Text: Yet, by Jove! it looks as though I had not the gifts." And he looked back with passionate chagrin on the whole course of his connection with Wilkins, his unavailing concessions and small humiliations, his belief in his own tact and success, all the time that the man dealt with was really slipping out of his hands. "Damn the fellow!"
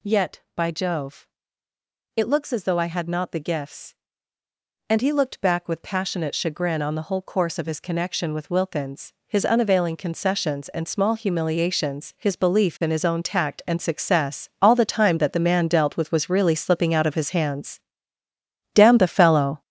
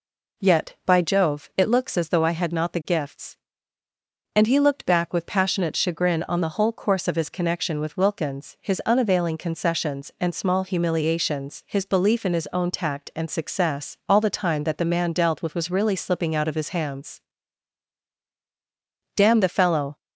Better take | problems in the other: second | gets louder; strong; throughout; 8 dB

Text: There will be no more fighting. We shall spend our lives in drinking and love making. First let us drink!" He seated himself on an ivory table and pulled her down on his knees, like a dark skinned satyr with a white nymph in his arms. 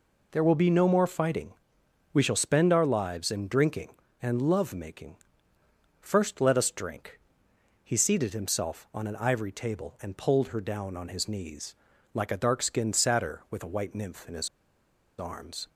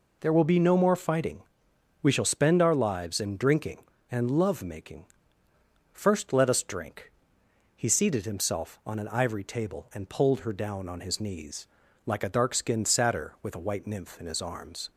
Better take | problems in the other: second | pauses between "his" and "arms"; noticeable; at 14.4 s; 0.71 s long

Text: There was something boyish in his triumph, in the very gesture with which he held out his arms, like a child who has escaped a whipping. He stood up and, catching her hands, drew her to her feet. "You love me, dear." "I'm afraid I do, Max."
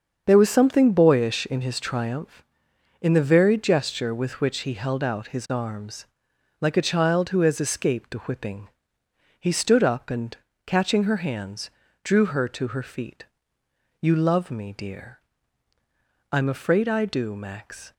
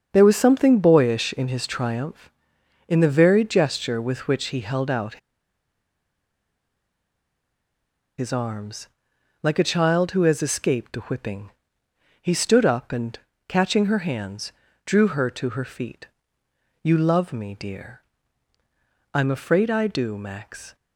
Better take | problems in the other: first | starts louder than the rest; until 1.1 s; 7 dB; also in the first // pauses between "out" and "his"; strong; at 5.1 s; 3.0 s long

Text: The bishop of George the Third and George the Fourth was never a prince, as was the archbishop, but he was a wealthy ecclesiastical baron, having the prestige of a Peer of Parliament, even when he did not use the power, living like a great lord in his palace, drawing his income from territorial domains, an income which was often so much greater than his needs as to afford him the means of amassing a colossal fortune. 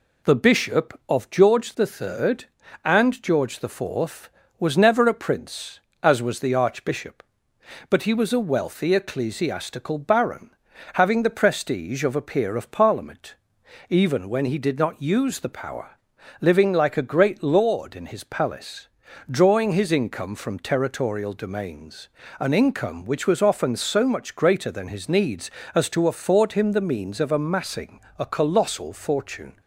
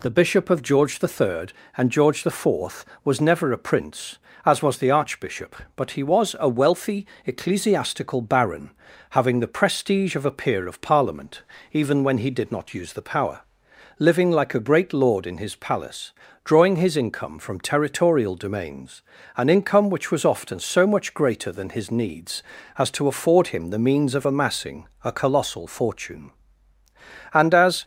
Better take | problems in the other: first | pauses between "wealthy" and "ecclesiastical"; slight; at 7.0 s; 0.20 s long // pauses between "amassing" and "a"; slight; at 24.8 s; 0.16 s long; slight in the first // goes on to say "And as"; from 27.3 s on; 0.50 s long

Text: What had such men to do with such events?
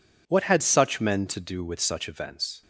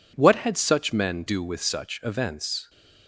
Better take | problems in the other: first | skips "to"; at 1.2 s

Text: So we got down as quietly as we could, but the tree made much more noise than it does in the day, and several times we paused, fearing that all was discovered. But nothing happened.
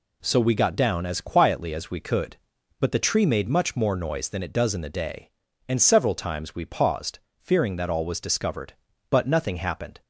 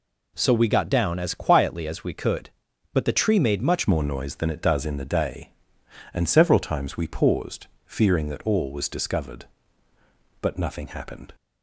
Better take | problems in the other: first | changes voice at "more"; from 3.8 s on; 7.5 s long

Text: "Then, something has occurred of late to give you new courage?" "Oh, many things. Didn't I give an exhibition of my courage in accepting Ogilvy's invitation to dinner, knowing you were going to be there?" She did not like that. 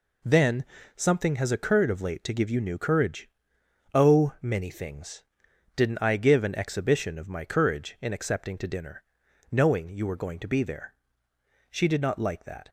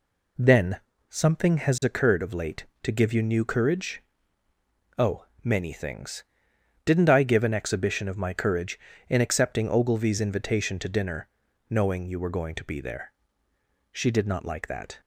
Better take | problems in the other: second | skips "Ogilvy's invitation"; at 8.5 s

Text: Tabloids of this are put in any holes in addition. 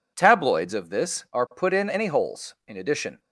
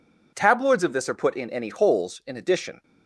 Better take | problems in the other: neither | none

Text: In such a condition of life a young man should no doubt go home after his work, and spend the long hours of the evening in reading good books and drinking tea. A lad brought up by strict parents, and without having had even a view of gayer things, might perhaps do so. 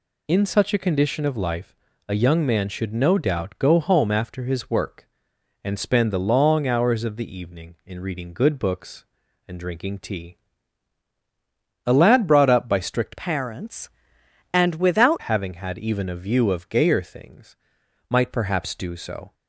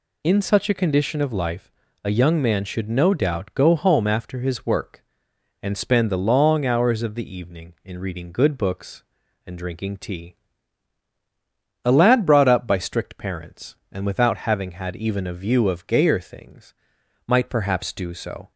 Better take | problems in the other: second | pauses between "life" and "a"; slight; at 1.7 s; 0.32 s long; slight in the second // changes voice from "parents" to "without"; from 13.1 to 15.2 s; 2.1 s long

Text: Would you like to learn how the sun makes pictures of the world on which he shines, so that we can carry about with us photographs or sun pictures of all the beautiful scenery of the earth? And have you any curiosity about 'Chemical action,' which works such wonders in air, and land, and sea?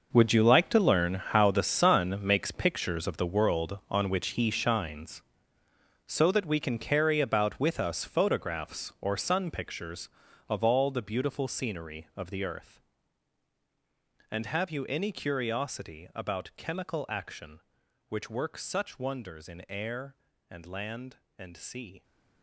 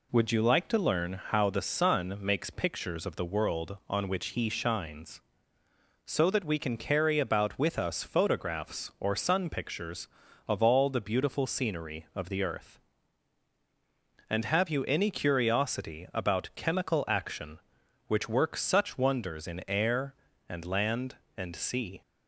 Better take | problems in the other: second | gets quieter; strong; throughout; 14 dB

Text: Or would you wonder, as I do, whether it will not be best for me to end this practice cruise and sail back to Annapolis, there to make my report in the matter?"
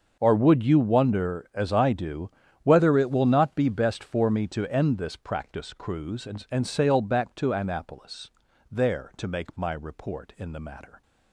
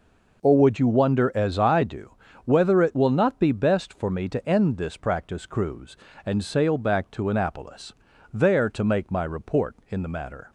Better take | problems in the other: second | starts louder than the rest; until 1.2 s; 6.5 dB // says "and" twice; at 6.4 s

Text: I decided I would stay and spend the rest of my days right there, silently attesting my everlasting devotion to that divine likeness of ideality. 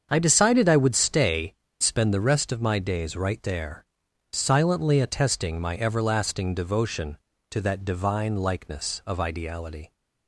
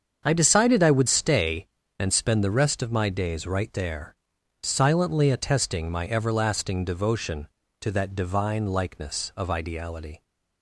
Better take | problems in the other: second | starts louder than the rest; until 1.1 s; 7 dB; also in the second // skips "and"; at 1.6 s

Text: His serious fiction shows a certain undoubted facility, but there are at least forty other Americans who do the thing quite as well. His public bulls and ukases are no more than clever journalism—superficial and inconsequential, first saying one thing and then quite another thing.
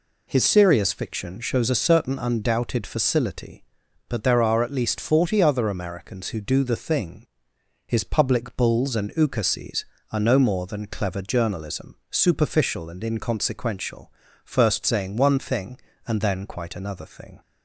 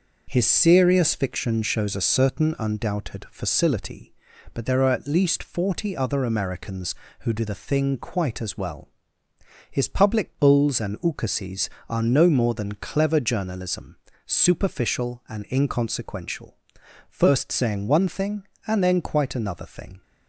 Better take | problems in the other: second | skips "quite as well"; at 7.5 s

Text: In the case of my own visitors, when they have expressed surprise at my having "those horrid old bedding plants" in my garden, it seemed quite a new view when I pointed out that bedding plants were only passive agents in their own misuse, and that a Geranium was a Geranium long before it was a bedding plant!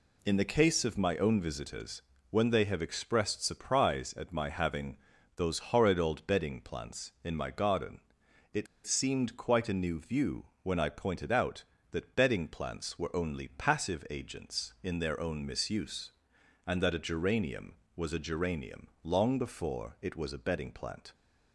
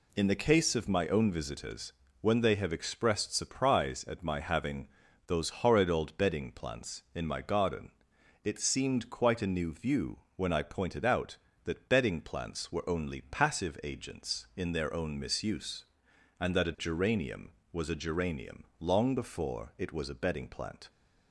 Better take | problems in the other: second | pauses between "having" and "those"; at 4.9 s; 0.38 s long; also in the second // pauses between "it" and "seemed"; slight; at 8.6 s; 0.19 s long // pauses between "view" and "when"; slight; at 10.4 s; 0.16 s long; slight in the second // pauses between "Geranium" and "long"; slight; at 18.8 s; 0.16 s long; slight in the second

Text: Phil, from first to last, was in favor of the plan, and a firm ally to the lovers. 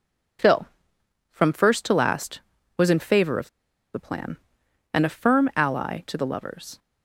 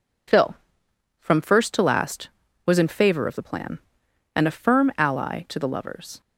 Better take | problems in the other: second | pauses between "of" and "the"; noticeable; at 3.4 s; 0.45 s long

